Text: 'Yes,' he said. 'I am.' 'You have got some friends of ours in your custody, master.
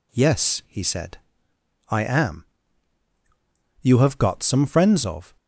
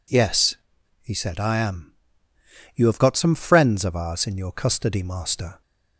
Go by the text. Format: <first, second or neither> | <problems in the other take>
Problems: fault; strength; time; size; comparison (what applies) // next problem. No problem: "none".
second | stops before "ours in your custody master"; at 5.3 s